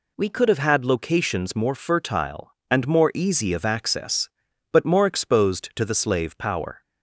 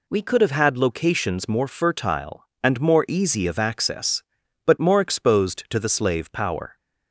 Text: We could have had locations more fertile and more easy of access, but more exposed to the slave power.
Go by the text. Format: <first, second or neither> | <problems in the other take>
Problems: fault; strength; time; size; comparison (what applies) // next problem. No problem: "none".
neither | none